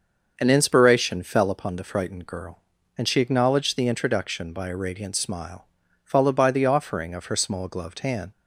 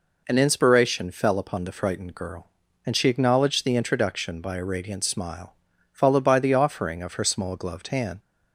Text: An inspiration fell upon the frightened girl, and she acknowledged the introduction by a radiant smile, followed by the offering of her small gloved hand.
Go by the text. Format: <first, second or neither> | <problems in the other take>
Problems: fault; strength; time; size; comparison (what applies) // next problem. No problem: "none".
second | starts louder than the rest; until 1.6 s; 6.5 dB